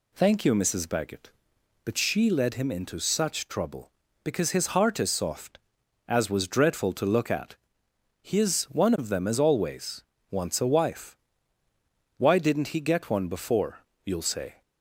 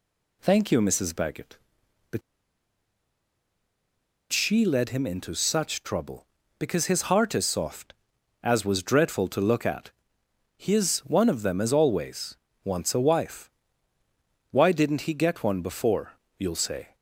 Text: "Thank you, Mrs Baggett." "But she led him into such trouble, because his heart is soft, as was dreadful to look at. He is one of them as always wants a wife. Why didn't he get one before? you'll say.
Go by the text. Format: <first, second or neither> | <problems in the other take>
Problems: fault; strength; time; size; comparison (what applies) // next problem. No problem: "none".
first | pauses between "But" and "she"; strong; at 2.2 s; 2.1 s long // pauses between "always" and "wants"; slight; at 12.3 s; 0.28 s long; slight in the first